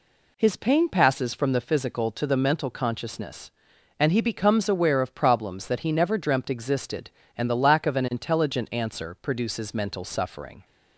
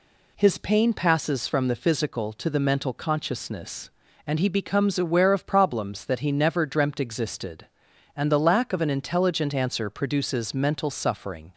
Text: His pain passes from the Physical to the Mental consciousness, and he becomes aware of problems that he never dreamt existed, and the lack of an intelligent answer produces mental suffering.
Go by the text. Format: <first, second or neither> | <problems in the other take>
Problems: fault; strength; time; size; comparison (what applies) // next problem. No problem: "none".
neither | none